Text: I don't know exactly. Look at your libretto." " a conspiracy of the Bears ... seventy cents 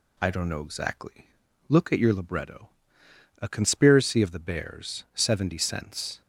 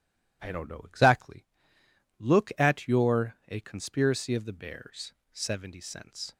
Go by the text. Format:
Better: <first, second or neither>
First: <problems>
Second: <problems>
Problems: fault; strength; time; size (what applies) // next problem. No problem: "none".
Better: first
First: none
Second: skips "libretto"; at 3.3 s